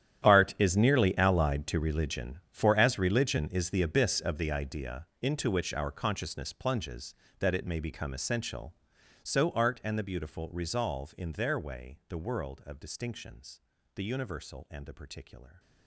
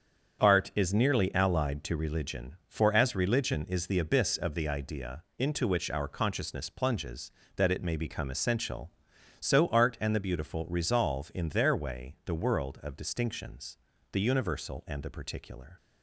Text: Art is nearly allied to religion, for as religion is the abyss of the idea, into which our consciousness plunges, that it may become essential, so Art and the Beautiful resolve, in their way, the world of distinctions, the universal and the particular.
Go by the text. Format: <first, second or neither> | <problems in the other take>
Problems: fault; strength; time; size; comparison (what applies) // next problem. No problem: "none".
second | gets quieter; strong; throughout; 16.5 dB // starts louder than the rest; strong; until 1.3 s; 10.5 dB; strong in the second